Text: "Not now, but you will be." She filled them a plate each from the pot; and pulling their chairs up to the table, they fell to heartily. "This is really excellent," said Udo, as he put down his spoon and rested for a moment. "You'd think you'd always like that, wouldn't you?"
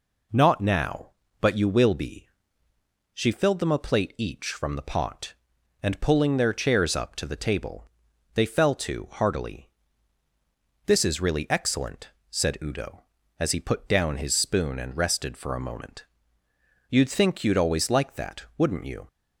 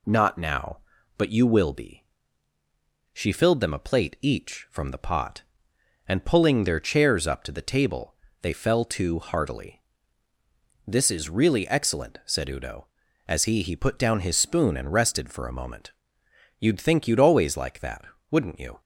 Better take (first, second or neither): first